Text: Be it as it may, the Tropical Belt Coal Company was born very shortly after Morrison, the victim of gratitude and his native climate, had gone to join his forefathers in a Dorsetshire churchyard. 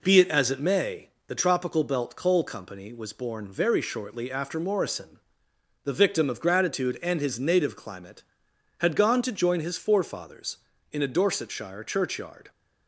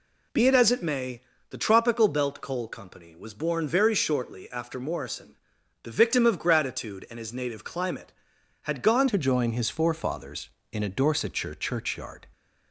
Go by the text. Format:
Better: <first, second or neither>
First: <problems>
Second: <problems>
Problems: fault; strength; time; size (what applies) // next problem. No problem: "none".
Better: first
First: none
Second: changes voice at "to"; from 9.0 s on; 3.2 s long